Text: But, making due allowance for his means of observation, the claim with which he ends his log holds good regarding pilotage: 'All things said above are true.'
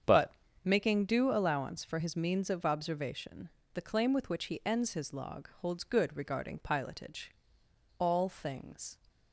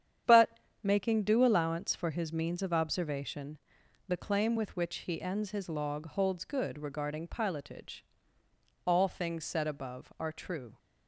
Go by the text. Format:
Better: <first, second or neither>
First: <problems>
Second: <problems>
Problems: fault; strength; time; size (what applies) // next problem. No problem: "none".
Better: second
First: starts louder than the rest; strong; until 1.3 s; 7.5 dB // stops before "said above are true"; at 9.0 s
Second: starts louder than the rest; strong; until 1.4 s; 9 dB